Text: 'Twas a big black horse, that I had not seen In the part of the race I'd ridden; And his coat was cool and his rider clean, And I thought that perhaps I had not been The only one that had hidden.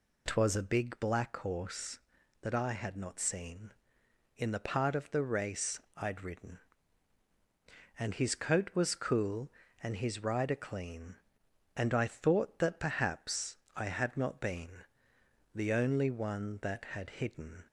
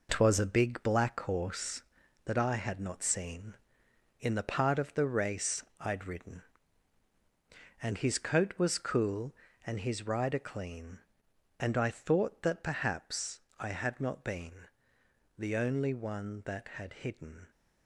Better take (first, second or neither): first